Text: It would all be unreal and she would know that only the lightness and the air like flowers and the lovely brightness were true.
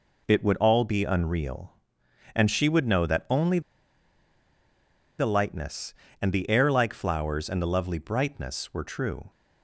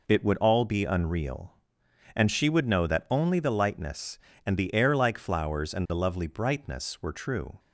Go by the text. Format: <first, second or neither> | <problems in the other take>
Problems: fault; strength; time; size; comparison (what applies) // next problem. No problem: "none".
second | pauses between "only" and "the"; strong; at 3.6 s; 1.5 s long